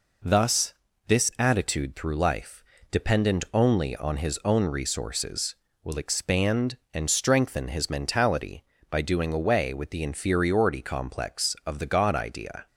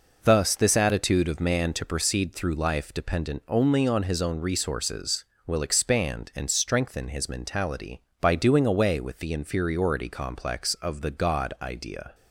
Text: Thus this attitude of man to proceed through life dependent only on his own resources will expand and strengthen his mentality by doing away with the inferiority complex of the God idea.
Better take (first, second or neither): second